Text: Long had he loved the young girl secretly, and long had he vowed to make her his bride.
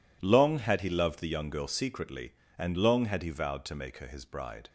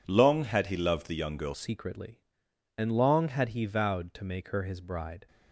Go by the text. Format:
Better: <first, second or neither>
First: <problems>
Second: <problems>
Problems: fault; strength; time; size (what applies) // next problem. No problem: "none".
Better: first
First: none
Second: changes voice at "secretly"; from 1.5 s on; 3.7 s long